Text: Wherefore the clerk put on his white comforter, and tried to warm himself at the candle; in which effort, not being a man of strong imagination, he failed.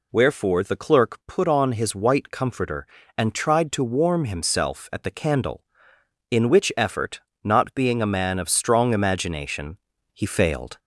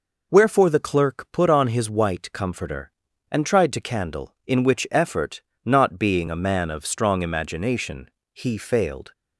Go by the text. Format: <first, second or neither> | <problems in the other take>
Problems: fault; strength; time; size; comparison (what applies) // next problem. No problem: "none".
first | skips "warm himself at the"; at 3.8 s